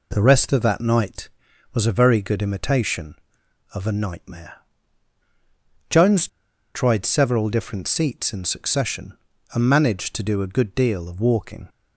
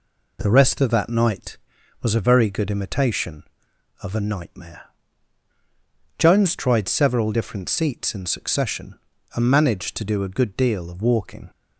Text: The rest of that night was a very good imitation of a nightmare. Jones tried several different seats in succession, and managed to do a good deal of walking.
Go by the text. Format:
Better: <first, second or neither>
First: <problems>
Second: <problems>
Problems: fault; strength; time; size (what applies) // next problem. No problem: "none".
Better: second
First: pauses between "Jones" and "tried"; noticeable; at 6.2 s; 0.46 s long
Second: none